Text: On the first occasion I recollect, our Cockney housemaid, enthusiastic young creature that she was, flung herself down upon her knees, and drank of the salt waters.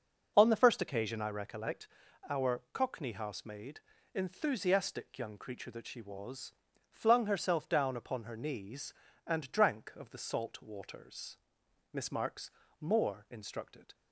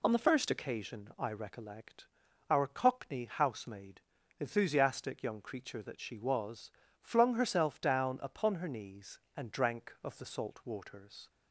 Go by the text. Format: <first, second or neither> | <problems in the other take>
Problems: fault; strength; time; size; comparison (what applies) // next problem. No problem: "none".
second | goes on to say "Miss Marks more instructed"; strong; from 11.9 s on; 2.0 s long